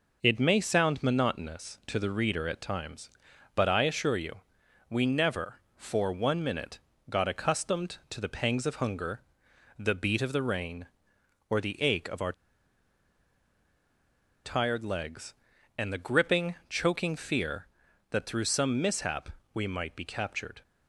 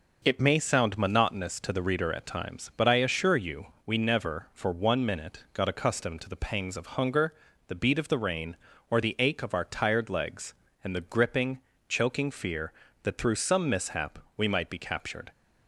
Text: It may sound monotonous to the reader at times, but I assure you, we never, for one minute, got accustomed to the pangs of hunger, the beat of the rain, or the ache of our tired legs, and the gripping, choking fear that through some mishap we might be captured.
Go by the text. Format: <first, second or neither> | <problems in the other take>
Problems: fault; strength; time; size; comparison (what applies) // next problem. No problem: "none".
second | pauses between "our" and "tired"; strong; at 12.3 s; 2.1 s long // pauses between "mishap" and "we"; slight; at 19.2 s; 0.22 s long; slight in the second